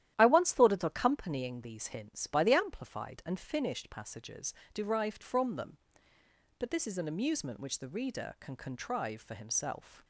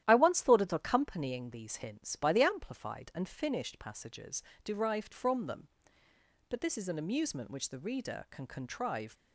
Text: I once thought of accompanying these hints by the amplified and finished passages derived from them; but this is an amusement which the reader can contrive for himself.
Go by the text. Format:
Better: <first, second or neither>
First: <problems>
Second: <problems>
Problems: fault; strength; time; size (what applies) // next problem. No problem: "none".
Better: first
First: starts louder than the rest; strong; until 1.1 s; 12 dB // pauses between "passages" and "derived"; slight; at 4.5 s; 0.20 s long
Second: starts louder than the rest; strong; until 1.0 s; 12 dB // pauses between "passages" and "derived"; slight; at 4.4 s; 0.22 s long // stops before "for himself"; at 9.1 s